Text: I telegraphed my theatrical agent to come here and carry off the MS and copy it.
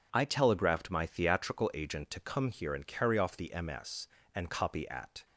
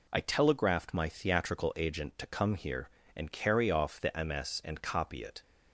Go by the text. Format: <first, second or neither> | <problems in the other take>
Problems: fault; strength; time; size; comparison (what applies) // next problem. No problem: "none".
second | says "at" for "it"; at 4.8 s